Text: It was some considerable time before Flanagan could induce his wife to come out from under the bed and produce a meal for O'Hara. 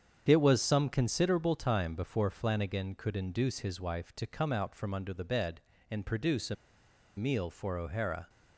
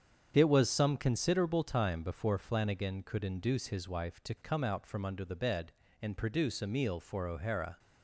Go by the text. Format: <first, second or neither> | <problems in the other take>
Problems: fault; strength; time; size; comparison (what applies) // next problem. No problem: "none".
second | starts louder than the rest; strong; until 1.2 s; 8 dB; strong in the second // pauses between "a" and "meal"; noticeable; at 6.5 s; 0.61 s long